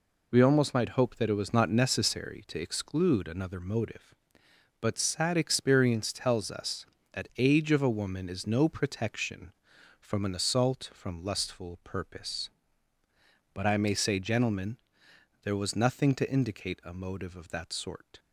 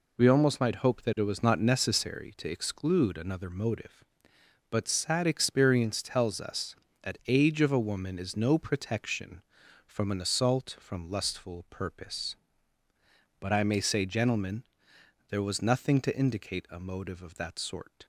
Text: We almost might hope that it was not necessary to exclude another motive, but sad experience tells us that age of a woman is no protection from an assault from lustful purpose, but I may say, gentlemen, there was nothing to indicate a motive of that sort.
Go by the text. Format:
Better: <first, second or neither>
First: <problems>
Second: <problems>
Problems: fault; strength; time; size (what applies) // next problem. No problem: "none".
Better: neither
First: none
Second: none